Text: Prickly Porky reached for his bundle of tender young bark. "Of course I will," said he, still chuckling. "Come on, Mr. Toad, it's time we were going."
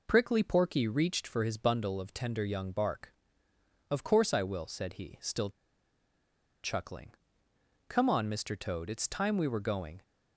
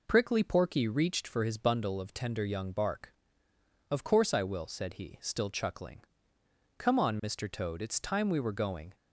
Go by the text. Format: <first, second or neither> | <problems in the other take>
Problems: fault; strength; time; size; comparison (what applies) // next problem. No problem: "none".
second | pauses between "still" and "chuckling"; at 5.4 s; 1.1 s long